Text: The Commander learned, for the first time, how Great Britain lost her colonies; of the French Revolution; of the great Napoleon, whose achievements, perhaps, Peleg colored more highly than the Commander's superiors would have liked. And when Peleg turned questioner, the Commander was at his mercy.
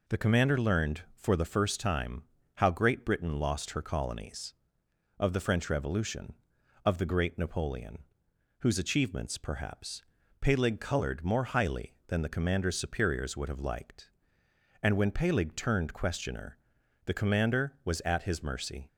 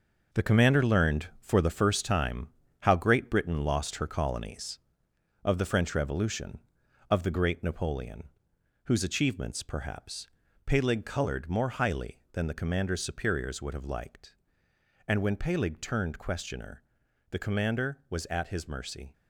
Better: first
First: none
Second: gets quieter; strong; throughout; 8.5 dB

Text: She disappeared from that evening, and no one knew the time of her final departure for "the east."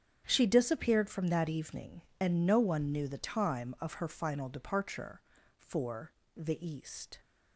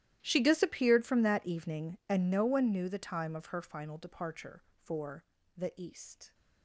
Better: first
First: starts louder than the rest; strong; until 1.2 s; 8.5 dB // pauses between "for" and "the"; slight; at 6.1 s; 0.22 s long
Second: gets quieter; strong; throughout; 23.5 dB // starts louder than the rest; strong; until 1.2 s; 13 dB // pauses between "for" and "the"; slight; at 5.2 s; 0.32 s long

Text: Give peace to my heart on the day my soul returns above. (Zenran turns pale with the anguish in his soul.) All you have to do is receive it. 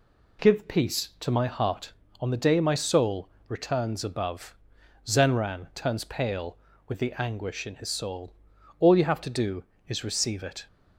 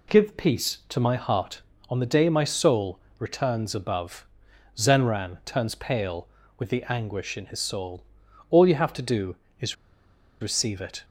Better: first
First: pauses between "soul" and "returns"; slight; at 3.2 s; 0.20 s long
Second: pauses between "soul" and "returns"; slight; at 2.9 s; 0.20 s long // pauses between "is" and "receive"; noticeable; at 9.7 s; 0.67 s long

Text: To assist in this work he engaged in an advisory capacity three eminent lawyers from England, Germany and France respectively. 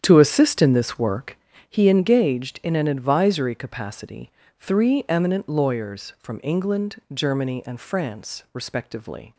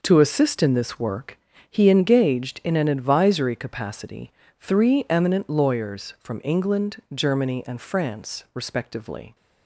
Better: second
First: starts louder than the rest; strong; until 1.7 s; 9 dB // pauses between "work" and "he"; slight; at 1.3 s; 0.32 s long // pauses between "capacity" and "three"; slight; at 4.3 s; 0.30 s long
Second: pauses between "work" and "he"; slight; at 1.3 s; 0.32 s long // pauses between "capacity" and "three"; slight; at 4.3 s; 0.30 s long

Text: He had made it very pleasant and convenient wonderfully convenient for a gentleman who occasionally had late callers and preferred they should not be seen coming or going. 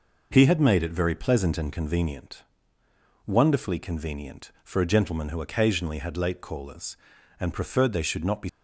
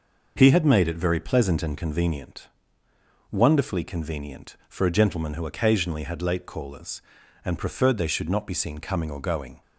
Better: second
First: pauses between "convenient" and "wonderfully"; noticeable; at 2.4 s; 0.82 s long // stops before "seen coming or going"; at 8.4 s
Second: pauses between "convenient" and "wonderfully"; noticeable; at 2.4 s; 0.82 s long

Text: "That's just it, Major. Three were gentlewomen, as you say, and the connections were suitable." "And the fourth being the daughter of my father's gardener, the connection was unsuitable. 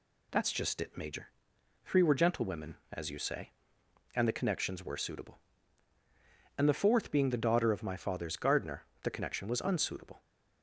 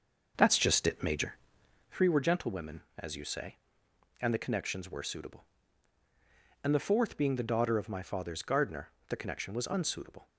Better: first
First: none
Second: starts louder than the rest; noticeable; until 2.0 s; 6 dB

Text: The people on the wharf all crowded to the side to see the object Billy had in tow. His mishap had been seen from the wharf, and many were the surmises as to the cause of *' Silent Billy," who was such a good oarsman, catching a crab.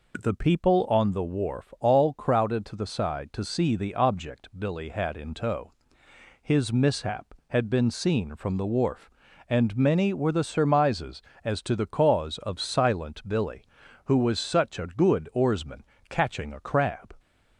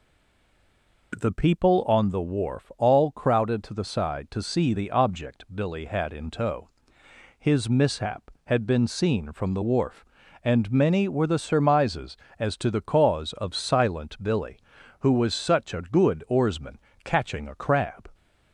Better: first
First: none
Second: stays silent before the first word; until 1.1 s; 1.1 s long

